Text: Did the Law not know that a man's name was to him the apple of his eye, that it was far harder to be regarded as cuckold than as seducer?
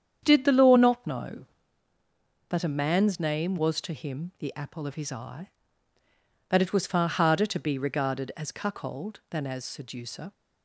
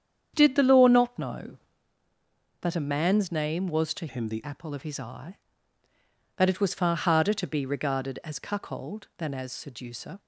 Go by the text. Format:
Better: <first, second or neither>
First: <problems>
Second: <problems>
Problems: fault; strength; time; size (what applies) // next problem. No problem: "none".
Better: first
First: starts louder than the rest; strong; until 1.2 s; 8.5 dB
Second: starts louder than the rest; strong; until 1.3 s; 8.5 dB // changes voice from "him" to "the"; from 4.0 to 4.4 s; 0.4 s long